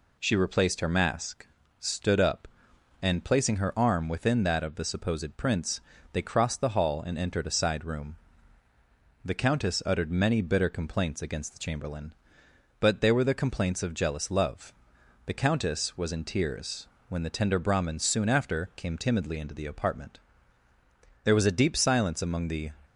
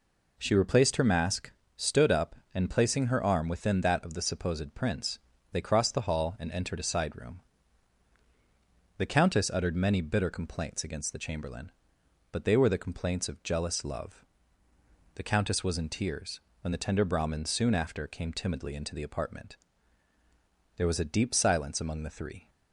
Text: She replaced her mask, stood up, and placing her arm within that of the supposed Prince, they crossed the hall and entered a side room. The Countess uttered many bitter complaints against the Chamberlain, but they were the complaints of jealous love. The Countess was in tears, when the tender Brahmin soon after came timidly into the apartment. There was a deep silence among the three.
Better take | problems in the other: second | stops before "three"; at 22.8 s

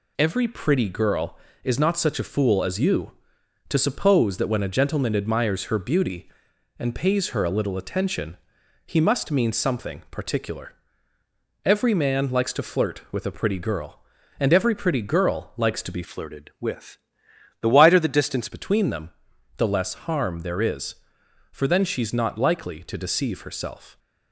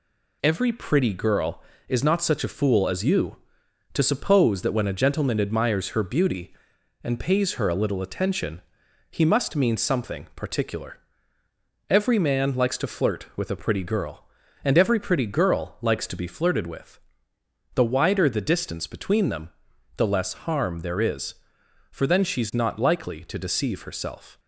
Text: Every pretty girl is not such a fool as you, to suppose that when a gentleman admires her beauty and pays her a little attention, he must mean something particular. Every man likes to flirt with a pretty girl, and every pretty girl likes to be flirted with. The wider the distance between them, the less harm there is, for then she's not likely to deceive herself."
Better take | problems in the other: second | changes voice from "flirted" to "distance"; from 16.0 to 18.4 s; 2.4 s long

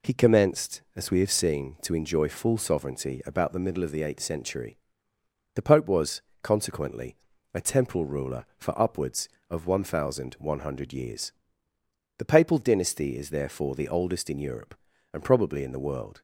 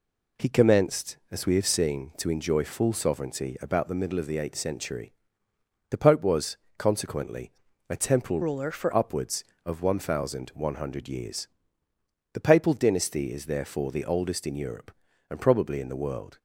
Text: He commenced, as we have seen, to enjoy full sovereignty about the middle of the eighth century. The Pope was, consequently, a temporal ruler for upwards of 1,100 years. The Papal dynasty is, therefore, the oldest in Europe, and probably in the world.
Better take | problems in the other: first | changes voice from "ruler" to "for"; from 8.4 to 8.9 s; 0.5 s long

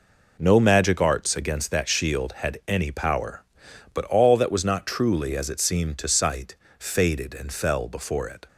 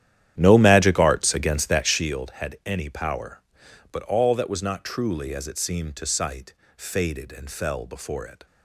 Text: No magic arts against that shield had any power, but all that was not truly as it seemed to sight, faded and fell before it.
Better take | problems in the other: first | starts louder than the rest; strong; until 2.1 s; 11 dB

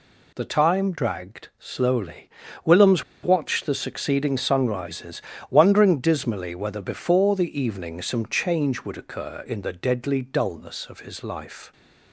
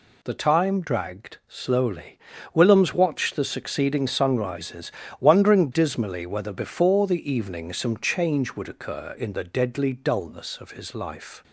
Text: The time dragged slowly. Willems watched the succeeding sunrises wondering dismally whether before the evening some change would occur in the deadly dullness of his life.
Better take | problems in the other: second | pauses between "Willems" and "watched"; slight; at 3.0 s; 0.20 s long // pauses between "sunrises" and "wondering"; slight; at 5.2 s; 0.28 s long; slight in the second

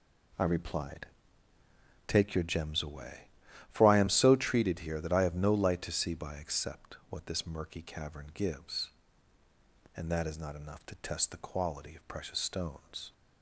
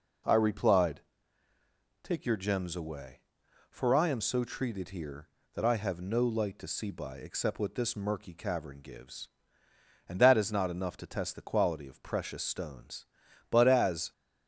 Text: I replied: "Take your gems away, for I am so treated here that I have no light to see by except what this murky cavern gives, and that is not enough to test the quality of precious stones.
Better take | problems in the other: first | goes on to say "But as"; noticeable; from 13.4 s on; 0.62 s long

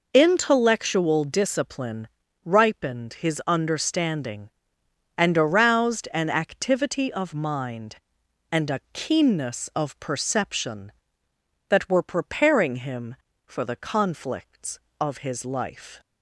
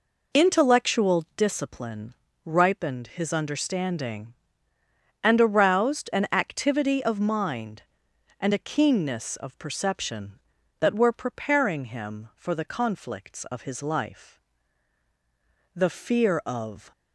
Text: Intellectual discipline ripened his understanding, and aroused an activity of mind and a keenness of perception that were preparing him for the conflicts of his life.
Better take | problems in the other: first | pauses between "discipline" and "ripened"; slight; at 2.1 s; 0.32 s long; slight in the first // goes on to say "The fear of"; noticeable; from 15.7 s on; 1.1 s long

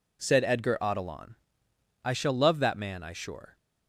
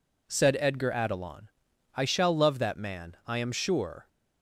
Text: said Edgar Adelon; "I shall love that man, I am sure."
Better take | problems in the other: second | skips "am"; at 3.1 s

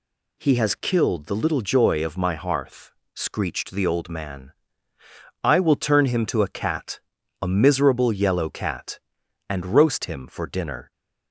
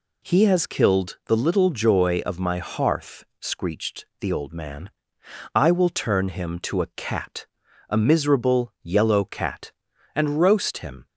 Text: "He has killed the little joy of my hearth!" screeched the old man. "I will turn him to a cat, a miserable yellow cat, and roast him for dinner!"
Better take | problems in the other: first | pauses between "screeched" and "the"; slight; at 4.0 s; 0.16 s long // stops before "for dinner"; at 11.0 s

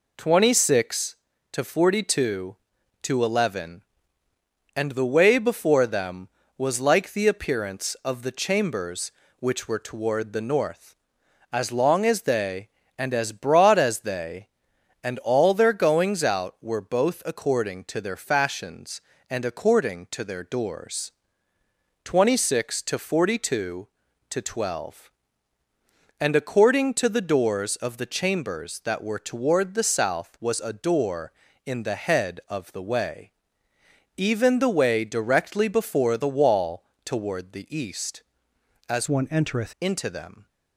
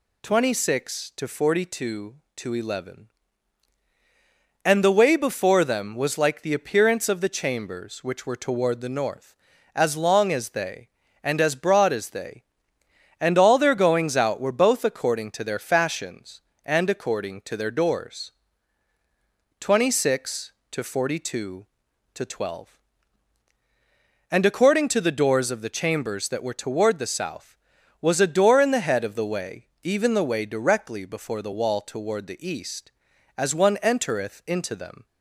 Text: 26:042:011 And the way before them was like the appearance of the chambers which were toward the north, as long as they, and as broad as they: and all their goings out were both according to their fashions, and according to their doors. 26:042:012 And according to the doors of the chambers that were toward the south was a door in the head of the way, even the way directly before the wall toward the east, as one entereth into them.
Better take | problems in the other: second | pauses between "wall" and "toward"; slight; at 36.8 s; 0.22 s long // changes voice from "one" to "entereth"; from 39.0 to 39.7 s; 0.7 s long

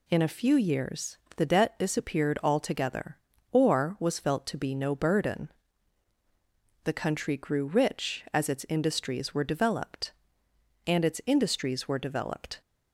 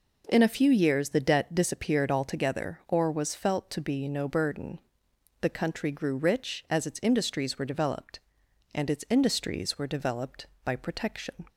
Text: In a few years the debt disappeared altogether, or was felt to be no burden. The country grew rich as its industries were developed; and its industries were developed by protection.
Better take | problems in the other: second | pauses between "years" and "the"; slight; at 1.1 s; 0.18 s long // stops before "by protection"; at 12.6 s

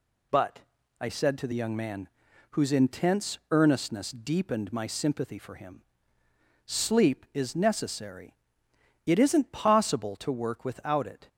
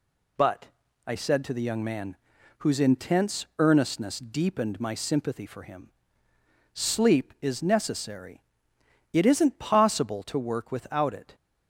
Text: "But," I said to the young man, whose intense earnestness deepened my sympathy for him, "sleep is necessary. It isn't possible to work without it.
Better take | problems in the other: neither | none

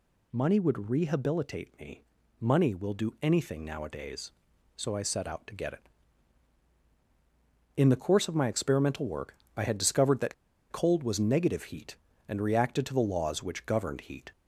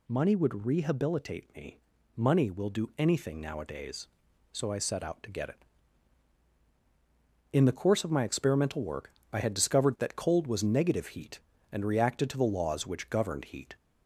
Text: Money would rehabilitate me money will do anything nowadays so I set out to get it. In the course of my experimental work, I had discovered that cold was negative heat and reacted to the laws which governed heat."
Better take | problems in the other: second | pauses between "me" and "money"; at 2.0 s; 0.38 s long; also in the second // pauses between "that" and "cold"; at 10.3 s; 0.36 s long

